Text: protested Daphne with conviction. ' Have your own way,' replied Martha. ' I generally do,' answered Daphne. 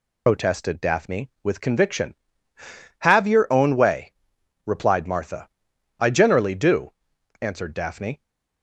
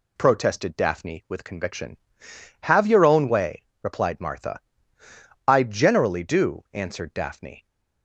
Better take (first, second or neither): second